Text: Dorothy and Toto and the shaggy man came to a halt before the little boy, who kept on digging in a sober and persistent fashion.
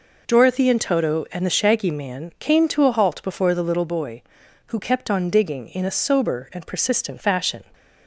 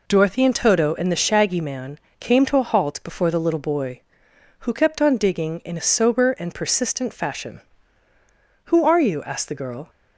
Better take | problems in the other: first | pauses between "man" and "came"; slight; at 1.9 s; 0.22 s long // goes on to say "Who are you asked the girl"; noticeable; from 8.6 s on; 1.2 s long

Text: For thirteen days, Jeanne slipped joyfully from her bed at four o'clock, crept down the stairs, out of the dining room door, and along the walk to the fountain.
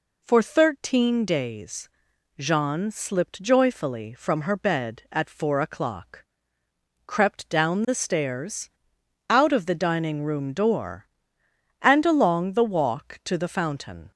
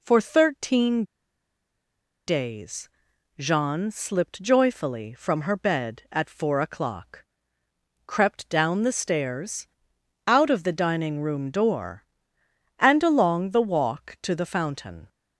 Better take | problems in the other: first | pauses between "thirteen" and "days"; at 1.0 s; 1.2 s long

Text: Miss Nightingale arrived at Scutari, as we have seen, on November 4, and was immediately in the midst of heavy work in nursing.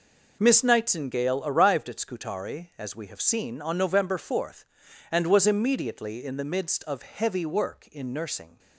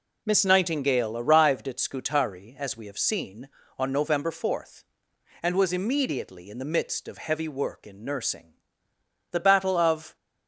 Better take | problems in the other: first | goes on to say "The Battle of"; noticeable; from 9.3 s on; 0.84 s long

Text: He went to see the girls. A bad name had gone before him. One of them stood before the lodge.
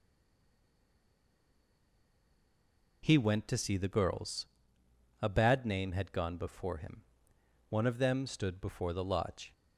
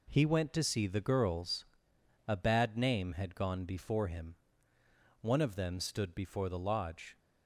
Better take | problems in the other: second | stays silent before the first word; strong; until 3.0 s; 3.0 s long

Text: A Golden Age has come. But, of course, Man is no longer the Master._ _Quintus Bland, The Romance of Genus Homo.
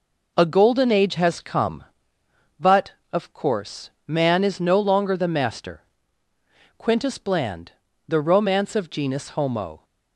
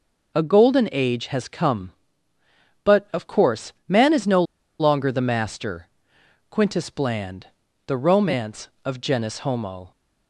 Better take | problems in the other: first | pauses between "no" and "longer"; at 4.4 s; 0.36 s long

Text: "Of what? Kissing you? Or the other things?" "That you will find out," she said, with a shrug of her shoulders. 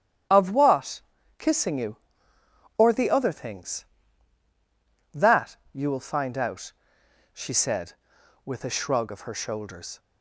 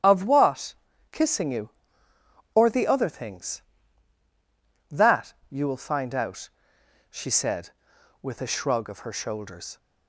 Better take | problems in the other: neither | starts louder than the rest; strong; the same in both // pauses between "That" and "you"; slight; the same in both

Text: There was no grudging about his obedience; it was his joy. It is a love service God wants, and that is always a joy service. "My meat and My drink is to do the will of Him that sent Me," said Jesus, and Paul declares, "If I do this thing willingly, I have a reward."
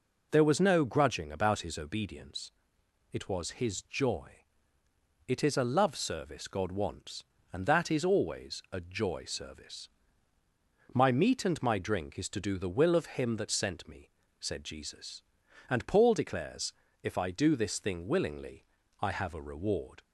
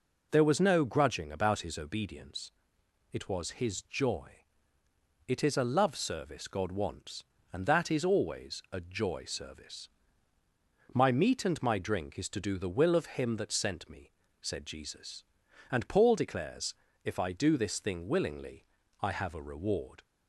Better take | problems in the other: neither | none

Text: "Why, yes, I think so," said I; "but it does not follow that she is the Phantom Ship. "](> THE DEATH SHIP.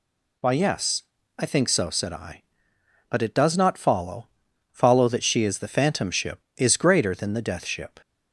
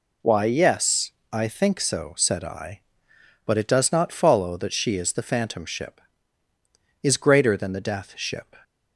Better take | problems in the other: second | says "follow" twice; at 4.6 s

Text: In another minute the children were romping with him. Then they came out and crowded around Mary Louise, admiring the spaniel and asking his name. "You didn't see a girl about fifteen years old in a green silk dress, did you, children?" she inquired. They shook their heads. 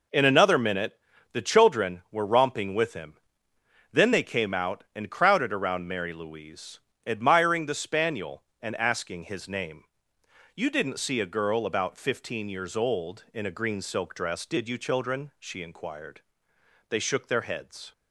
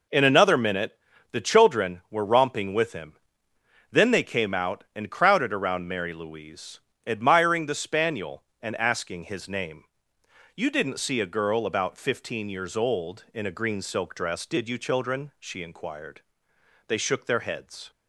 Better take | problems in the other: neither | pauses between "minute" and "the"; slight; the same in both

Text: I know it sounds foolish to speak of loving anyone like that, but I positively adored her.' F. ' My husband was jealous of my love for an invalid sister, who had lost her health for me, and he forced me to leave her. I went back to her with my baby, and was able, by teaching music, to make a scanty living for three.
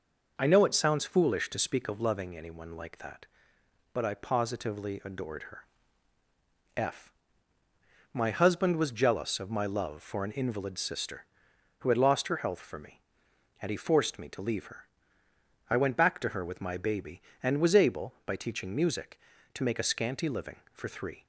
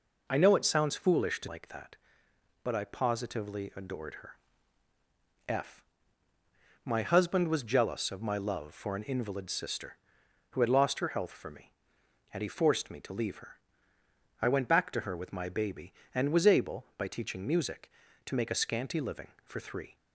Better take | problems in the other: first | skips "speak of loving anyone"; at 1.4 s

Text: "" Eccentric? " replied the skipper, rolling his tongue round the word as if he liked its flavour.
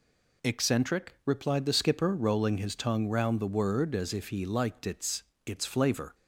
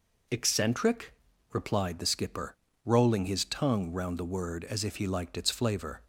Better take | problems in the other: second | says "its" twice; at 5.4 s

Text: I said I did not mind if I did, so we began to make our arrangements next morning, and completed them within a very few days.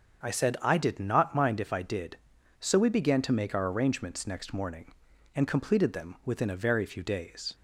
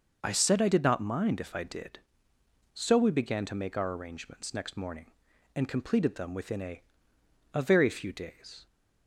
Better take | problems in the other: first | starts louder than the rest; until 1.2 s; 6 dB; also in the first // says "a" twice; at 7.5 s

